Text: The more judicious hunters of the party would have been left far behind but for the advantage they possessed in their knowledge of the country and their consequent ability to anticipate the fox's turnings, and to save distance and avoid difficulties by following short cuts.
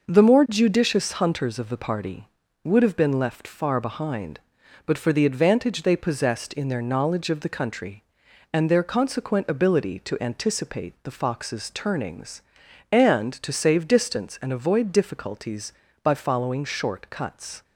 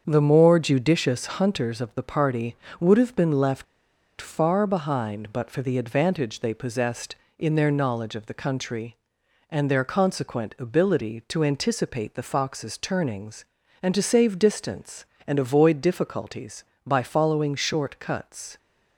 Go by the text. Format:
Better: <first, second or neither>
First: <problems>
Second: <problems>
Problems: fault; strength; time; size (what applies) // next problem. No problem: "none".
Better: first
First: none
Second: starts louder than the rest; until 1.0 s; 7 dB // pauses between "judicious" and "hunters"; slight; at 1.2 s; 0.16 s long // pauses between "left" and "far"; noticeable; at 3.6 s; 0.54 s long